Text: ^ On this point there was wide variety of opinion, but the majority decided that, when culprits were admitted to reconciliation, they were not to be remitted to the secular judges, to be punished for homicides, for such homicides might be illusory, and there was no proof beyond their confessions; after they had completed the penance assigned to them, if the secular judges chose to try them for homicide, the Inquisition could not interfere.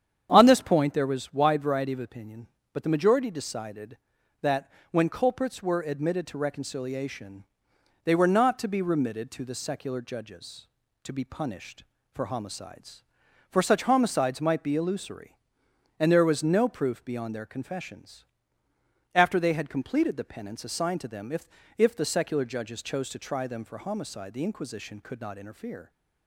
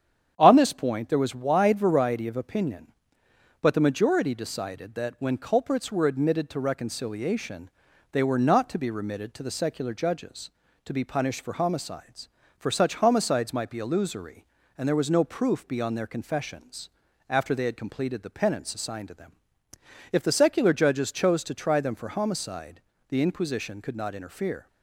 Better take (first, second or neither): second